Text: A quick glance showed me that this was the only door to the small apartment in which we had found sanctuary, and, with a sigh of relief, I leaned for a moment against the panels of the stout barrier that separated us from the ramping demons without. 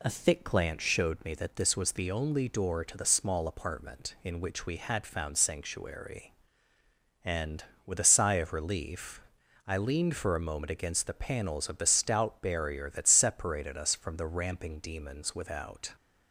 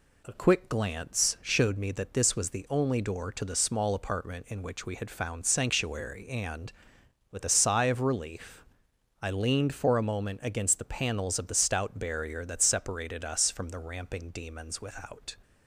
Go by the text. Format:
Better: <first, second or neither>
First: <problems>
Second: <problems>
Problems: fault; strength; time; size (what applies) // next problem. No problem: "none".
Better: second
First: says "thick" for "quick"; at 0.0 s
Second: none